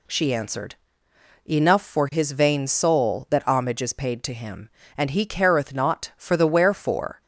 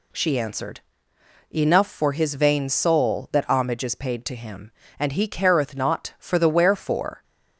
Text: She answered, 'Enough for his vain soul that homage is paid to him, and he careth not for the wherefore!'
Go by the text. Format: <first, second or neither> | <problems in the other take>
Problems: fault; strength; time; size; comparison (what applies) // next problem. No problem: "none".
neither | none